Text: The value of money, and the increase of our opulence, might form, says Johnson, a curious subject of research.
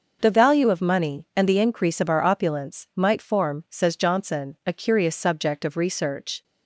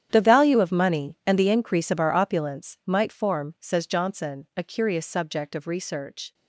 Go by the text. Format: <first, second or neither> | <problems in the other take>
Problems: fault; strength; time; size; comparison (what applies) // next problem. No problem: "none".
first | gets quieter; strong; throughout; 16.5 dB